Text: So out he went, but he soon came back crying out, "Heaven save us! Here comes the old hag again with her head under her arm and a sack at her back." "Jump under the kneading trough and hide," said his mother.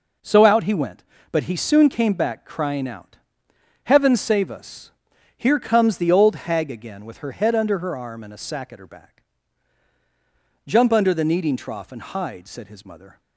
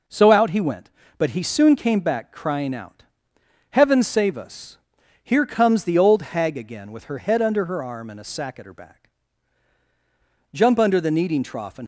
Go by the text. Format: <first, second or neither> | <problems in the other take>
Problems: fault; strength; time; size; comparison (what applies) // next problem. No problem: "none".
first | stops before "hide said his mother"; at 11.8 s